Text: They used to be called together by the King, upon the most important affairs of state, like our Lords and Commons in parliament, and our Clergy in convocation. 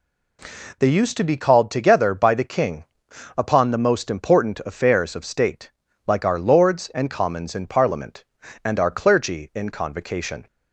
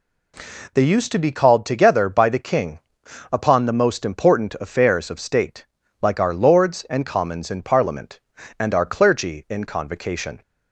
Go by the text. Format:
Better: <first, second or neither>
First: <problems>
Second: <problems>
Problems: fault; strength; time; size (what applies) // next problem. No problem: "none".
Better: neither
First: none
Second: none